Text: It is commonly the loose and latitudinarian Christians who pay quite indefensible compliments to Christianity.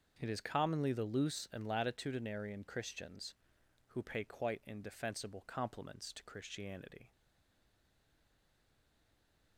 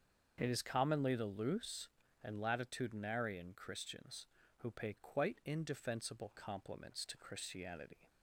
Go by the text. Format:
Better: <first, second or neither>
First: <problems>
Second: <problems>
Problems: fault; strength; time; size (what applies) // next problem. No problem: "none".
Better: second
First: starts louder than the rest; until 1.2 s; 6.5 dB // stays silent after the last word; from 7.1 s on; 2.4 s long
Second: starts louder than the rest; until 1.3 s; 7 dB